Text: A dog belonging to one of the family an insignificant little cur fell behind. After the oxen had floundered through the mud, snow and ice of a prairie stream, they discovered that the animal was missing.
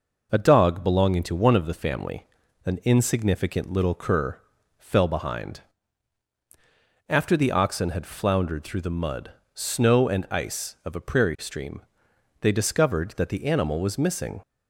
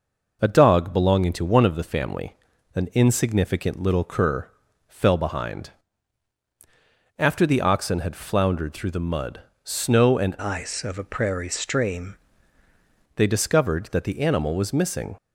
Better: first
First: pauses between "family" and "an"; at 2.2 s; 0.38 s long // pauses between "cur" and "fell"; at 4.3 s; 0.40 s long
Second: pauses between "family" and "an"; at 2.3 s; 0.38 s long // pauses between "cur" and "fell"; at 4.4 s; 0.40 s long // changes voice from "ice" to "stream"; from 10.4 to 12.1 s; 1.7 s long

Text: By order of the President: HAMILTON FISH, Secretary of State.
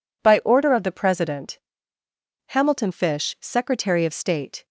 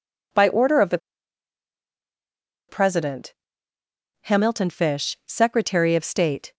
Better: first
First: none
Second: pauses between "the" and "President"; strong; at 0.9 s; 1.7 s long

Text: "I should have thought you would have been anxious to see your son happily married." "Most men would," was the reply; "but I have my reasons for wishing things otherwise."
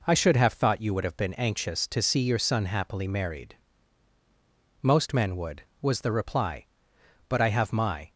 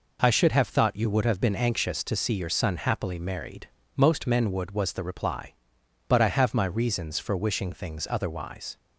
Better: second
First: stops before "reasons for wishing things otherwise"; at 8.0 s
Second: none

